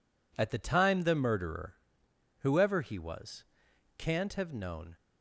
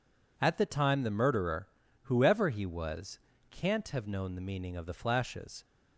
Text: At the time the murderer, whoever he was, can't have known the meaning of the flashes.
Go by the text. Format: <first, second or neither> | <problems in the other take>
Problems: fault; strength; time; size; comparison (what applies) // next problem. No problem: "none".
second | stops before "the meaning of the flashes"; at 4.9 s